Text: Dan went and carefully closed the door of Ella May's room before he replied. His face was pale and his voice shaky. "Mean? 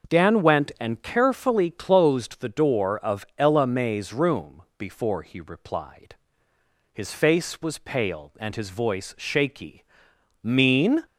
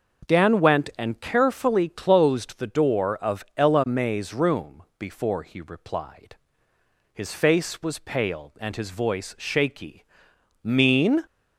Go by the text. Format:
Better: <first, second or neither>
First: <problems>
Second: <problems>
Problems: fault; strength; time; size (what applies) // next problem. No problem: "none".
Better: neither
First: none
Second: none